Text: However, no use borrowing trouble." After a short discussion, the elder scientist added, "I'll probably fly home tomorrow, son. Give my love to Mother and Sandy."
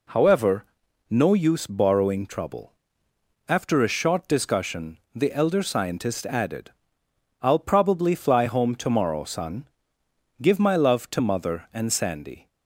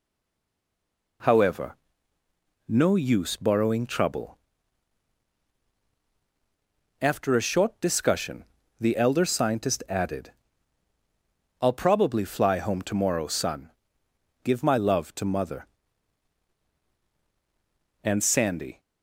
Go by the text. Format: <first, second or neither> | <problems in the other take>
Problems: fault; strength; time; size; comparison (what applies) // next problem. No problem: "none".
first | stays silent before the first word; noticeable; until 1.2 s; 1.2 s long